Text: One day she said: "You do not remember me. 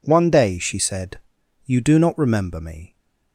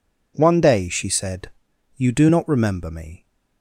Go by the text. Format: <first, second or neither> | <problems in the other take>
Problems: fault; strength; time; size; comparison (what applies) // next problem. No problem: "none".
neither | none